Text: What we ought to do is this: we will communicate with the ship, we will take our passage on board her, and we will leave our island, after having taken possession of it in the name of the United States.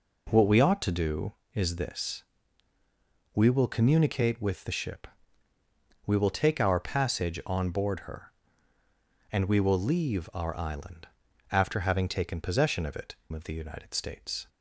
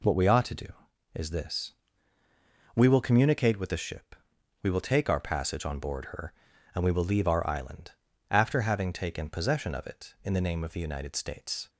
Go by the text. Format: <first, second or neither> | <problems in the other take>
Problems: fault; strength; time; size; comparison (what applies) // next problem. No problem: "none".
second | skips "in the name"; at 13.2 s